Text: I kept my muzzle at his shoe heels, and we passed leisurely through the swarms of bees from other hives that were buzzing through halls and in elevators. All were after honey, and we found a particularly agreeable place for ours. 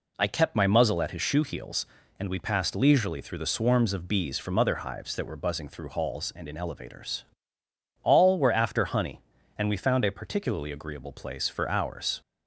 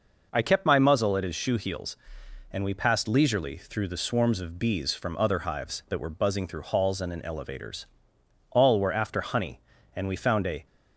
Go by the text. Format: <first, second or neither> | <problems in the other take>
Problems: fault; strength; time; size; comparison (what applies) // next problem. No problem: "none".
first | stops before "particularly agreeable place for ours"; at 10.6 s